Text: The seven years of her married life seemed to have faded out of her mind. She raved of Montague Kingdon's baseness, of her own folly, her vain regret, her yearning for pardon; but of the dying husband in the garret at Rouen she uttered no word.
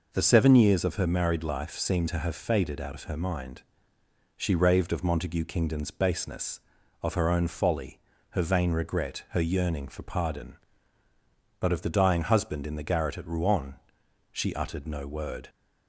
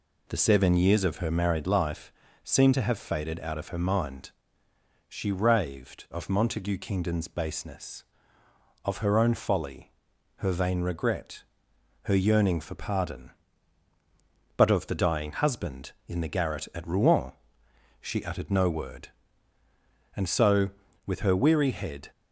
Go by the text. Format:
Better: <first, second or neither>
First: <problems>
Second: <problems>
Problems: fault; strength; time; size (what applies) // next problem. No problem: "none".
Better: first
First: pauses between "Rouen" and "she"; noticeable; at 13.7 s; 0.56 s long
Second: pauses between "life" and "seemed"; slight; at 2.1 s; 0.32 s long // pauses between "Rouen" and "she"; noticeable; at 17.3 s; 0.70 s long // goes on to say "And so with her weary head"; strong; from 20.1 s on; 1.9 s long